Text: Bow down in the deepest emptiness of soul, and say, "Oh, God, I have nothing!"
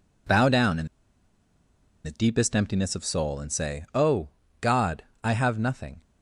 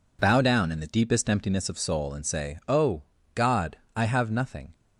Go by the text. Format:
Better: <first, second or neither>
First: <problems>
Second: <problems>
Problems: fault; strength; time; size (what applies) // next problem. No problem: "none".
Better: second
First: pauses between "in" and "the"; at 0.8 s; 1.1 s long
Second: none